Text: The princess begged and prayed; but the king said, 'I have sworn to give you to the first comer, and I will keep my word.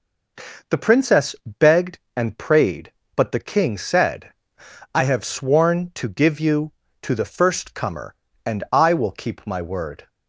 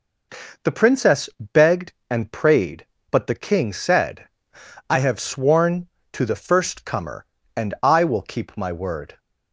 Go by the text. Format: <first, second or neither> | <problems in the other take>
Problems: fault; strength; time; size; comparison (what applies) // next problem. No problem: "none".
first | skips "to give you"; at 5.9 s